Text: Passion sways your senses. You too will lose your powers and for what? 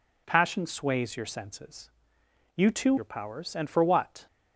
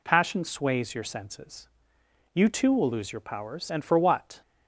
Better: second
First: skips "will lose"; at 2.9 s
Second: none

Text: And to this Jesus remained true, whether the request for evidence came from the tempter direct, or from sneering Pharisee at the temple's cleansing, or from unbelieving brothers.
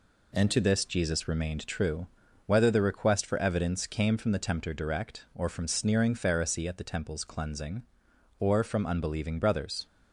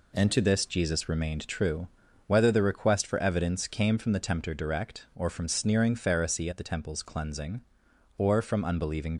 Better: first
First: none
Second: stops before "brothers"; at 9.1 s

